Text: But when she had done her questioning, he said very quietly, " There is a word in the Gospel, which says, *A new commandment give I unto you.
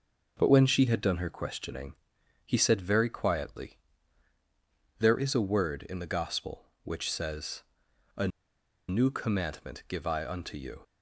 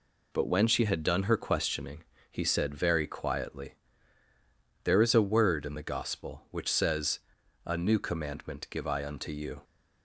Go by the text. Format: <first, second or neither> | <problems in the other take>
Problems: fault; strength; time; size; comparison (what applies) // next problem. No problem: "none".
second | pauses between "A" and "new"; noticeable; at 8.2 s; 0.60 s long